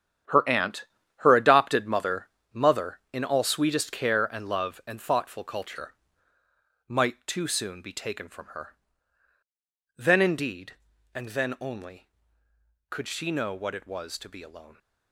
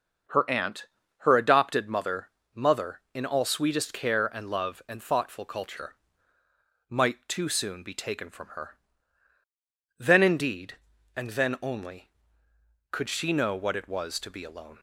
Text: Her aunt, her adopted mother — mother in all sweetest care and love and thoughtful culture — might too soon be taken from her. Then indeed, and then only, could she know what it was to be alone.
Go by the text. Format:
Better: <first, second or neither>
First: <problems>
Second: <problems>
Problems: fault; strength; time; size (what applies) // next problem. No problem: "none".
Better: second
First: gets quieter; strong; throughout; 11 dB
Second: none